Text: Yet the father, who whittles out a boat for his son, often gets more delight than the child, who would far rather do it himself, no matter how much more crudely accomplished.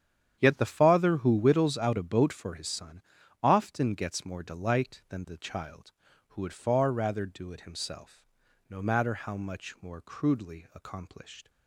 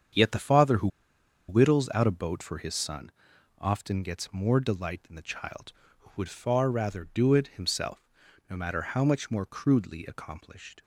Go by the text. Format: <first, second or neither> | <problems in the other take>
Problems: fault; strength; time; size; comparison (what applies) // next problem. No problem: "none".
first | starts louder than the rest; strong; until 1.7 s; 8 dB; strong in the first // pauses between "who" and "whittles"; noticeable; at 0.8 s; 0.60 s long